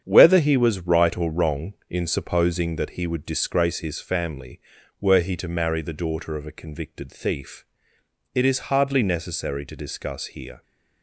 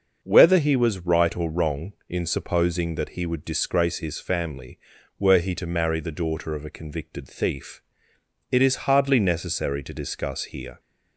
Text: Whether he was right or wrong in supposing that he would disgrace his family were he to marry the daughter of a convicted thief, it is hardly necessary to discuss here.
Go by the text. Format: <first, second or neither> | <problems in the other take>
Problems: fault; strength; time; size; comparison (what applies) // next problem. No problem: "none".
second | gets quieter; throughout; 7 dB // starts louder than the rest; strong; until 1.0 s; 8 dB; also in the second